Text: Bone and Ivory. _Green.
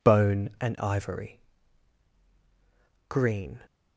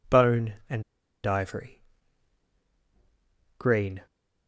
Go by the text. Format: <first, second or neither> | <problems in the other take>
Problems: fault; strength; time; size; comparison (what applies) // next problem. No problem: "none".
first | pauses between "and" and "Ivory"; at 0.8 s; 0.42 s long